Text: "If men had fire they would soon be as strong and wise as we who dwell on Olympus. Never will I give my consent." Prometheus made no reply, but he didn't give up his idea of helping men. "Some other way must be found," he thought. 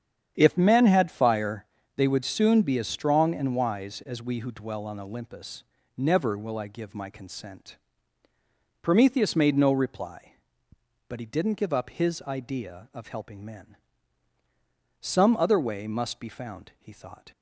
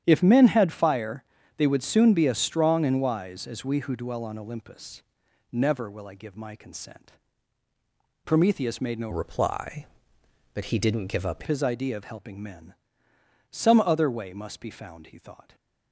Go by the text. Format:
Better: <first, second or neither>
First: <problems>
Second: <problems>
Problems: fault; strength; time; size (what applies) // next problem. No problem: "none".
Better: first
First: starts louder than the rest; strong; until 1.3 s; 8.5 dB // pauses between "fire" and "they"; slight; at 1.6 s; 0.32 s long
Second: starts louder than the rest; strong; until 1.0 s; 10 dB // pauses between "fire" and "they"; slight; at 1.2 s; 0.32 s long // changes voice from "reply" to "up"; from 9.1 to 11.4 s; 2.3 s long // stays silent after the last word; slight; from 15.4 s on; 0.5 s long